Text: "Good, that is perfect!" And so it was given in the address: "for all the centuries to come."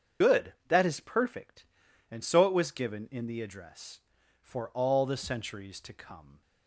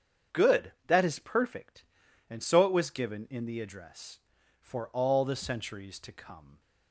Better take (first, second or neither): second